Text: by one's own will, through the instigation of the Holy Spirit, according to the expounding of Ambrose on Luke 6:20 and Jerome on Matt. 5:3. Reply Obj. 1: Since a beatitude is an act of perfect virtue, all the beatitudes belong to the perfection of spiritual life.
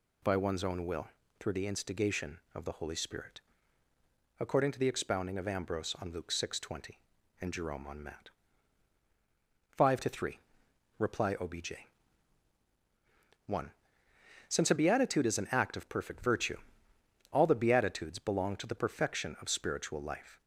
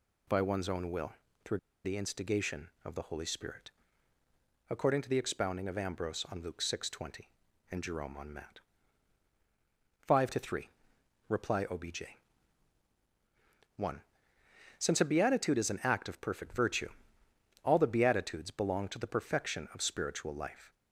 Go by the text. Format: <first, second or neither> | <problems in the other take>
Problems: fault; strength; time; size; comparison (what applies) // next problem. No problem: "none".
first | pauses between "through" and "the"; slight; at 1.5 s; 0.26 s long